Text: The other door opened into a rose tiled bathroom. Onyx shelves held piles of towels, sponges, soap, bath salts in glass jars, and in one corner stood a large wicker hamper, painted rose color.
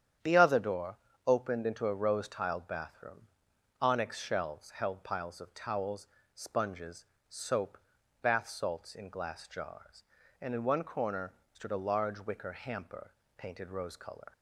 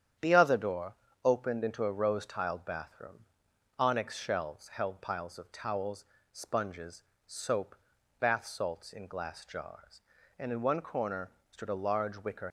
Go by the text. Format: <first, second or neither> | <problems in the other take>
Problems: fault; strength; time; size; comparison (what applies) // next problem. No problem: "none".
first | starts louder than the rest; strong; until 1.4 s; 9 dB; strong in the first // pauses between "door" and "opened"; slight; at 0.9 s; 0.28 s long; slight in the first // pauses between "corner" and "stood"; slight; at 11.2 s; 0.22 s long; slight in the first // stops before "hamper painted rose color"; at 12.4 s